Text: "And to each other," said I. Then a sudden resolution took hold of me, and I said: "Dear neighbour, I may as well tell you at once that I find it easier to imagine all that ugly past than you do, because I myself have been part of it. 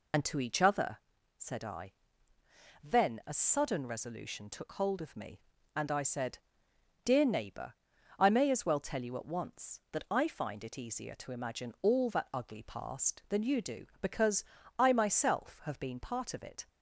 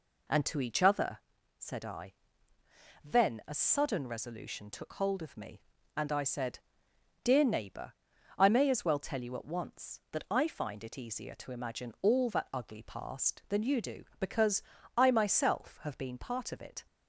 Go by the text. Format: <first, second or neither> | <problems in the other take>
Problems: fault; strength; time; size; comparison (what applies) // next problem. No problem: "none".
second | loses the start of "And"; at 0.1 s; 60 ms // pauses between "because" and "I"; slight; at 14.4 s; 0.34 s long; slight in the second